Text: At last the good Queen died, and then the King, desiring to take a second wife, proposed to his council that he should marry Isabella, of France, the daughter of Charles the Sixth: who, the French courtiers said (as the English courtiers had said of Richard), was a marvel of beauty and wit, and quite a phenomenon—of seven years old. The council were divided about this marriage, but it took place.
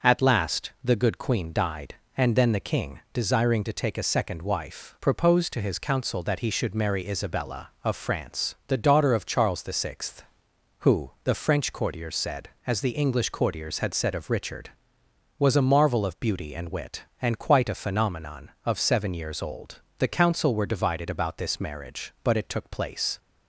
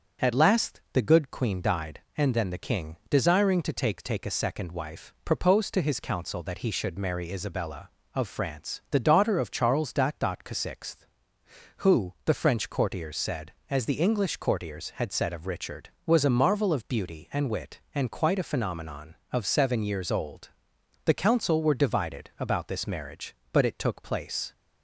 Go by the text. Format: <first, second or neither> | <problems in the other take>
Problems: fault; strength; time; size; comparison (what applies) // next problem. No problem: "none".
first | starts louder than the rest; until 1.3 s; 7 dB; noticeable in the first // says "take" twice; at 4.0 s // pauses between "the" and "Sixth"; slight; at 10.3 s; 0.16 s long